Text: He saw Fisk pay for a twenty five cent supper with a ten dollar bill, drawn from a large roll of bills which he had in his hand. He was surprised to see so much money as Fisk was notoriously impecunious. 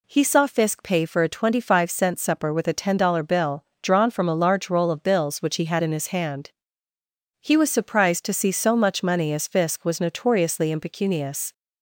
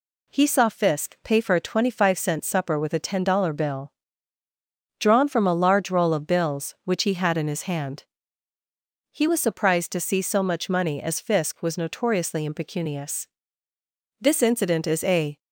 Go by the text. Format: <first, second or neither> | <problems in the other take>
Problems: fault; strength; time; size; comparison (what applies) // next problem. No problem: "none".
first | goes on to say "This incident is a"; noticeable; from 14.1 s on; 1.1 s long